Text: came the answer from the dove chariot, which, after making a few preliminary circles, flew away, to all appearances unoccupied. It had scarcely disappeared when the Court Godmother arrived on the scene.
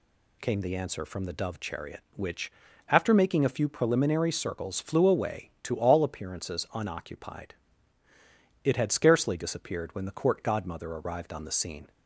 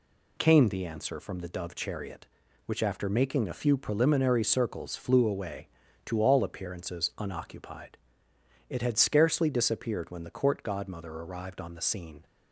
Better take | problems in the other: neither | none

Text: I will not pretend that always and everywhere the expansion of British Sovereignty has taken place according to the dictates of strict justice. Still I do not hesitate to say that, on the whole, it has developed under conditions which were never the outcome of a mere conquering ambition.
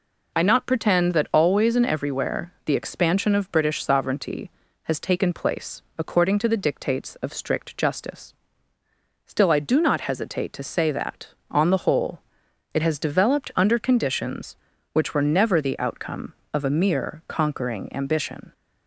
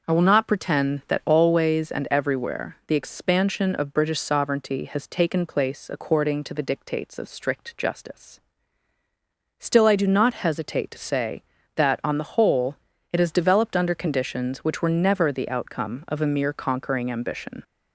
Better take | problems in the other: second | skips "will"; at 0.4 s // pauses between "place" and "according"; slight; at 5.8 s; 0.16 s long

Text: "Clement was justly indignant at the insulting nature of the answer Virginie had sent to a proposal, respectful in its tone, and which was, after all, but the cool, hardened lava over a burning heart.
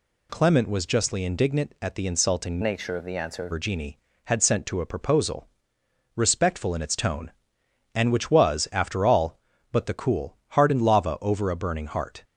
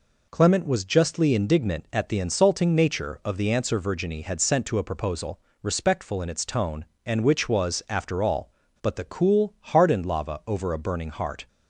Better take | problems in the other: second | changes voice from "nature" to "answer"; from 2.6 to 3.4 s; 0.8 s long

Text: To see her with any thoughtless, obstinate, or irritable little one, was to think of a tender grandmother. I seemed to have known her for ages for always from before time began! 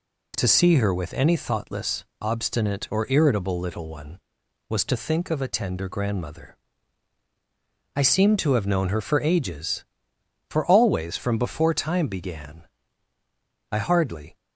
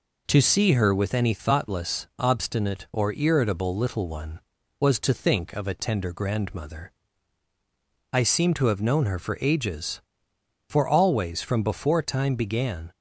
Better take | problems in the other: second | goes on to say "I hardly"; noticeable; from 13.7 s on; 0.64 s long

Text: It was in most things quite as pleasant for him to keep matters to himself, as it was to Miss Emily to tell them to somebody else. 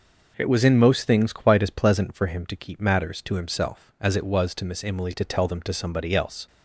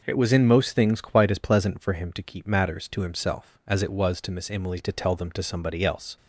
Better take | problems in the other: neither | none

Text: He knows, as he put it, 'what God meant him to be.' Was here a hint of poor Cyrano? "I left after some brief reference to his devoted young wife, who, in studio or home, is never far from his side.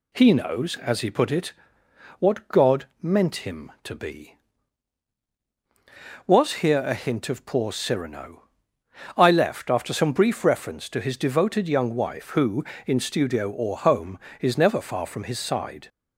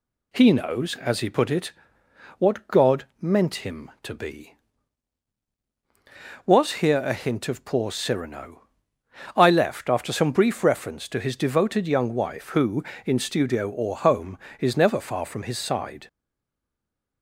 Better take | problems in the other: first | stays silent after the last word; from 16.0 s on; 1.2 s long

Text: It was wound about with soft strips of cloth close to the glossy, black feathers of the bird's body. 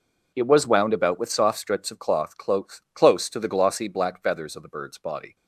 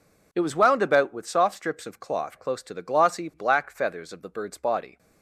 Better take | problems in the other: second | says "close" twice; at 2.9 s

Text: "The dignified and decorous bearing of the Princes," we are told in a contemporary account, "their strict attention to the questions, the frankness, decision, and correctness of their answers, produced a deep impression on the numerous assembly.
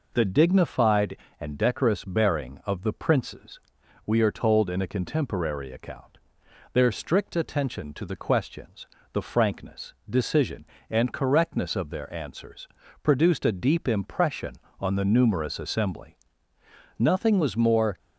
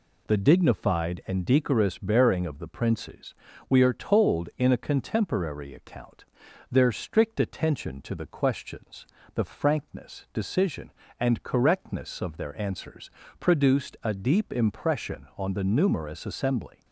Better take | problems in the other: second | goes on to say "Nothing was more"; noticeable; from 16.9 s on; 1.0 s long

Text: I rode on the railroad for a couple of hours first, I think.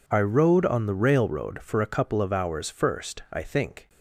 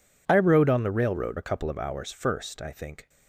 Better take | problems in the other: first | skips "for"; at 1.3 s

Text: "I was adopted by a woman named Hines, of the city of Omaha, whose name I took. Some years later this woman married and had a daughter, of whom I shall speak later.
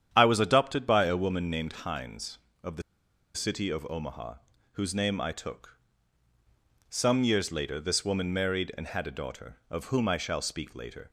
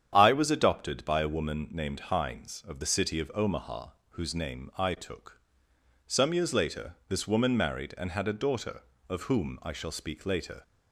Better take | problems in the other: second | starts louder than the rest; strong; until 1.1 s; 9 dB; strong in the second // pauses between "the" and "city"; noticeable; at 2.8 s; 0.53 s long

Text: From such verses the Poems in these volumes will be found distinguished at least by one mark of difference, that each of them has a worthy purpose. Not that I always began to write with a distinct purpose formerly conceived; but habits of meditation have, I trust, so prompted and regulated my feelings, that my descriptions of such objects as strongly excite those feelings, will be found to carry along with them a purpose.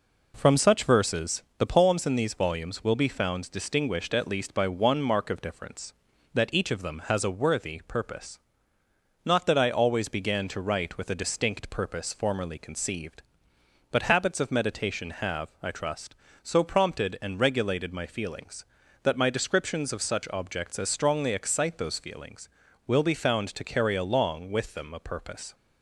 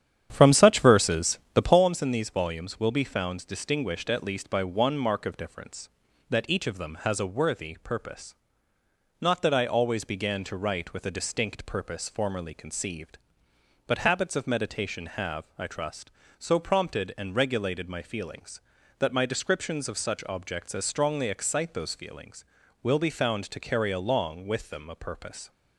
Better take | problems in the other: first | starts louder than the rest; strong; until 1.9 s; 9.5 dB // pauses between "verses" and "the"; slight; at 1.3 s; 0.16 s long; slight in the first

